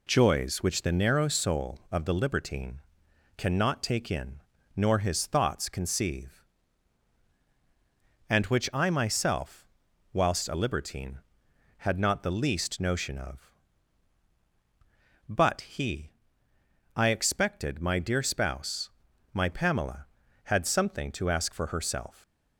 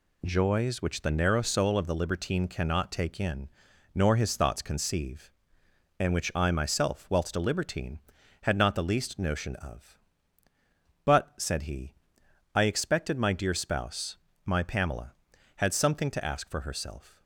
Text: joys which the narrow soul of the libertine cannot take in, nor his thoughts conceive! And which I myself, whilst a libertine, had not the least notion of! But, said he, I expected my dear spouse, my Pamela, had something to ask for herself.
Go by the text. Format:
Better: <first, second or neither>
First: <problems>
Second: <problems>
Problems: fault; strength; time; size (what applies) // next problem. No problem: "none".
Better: second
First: pauses between "libertine" and "cannot"; noticeable; at 2.7 s; 0.56 s long // skips "said"; at 15.6 s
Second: none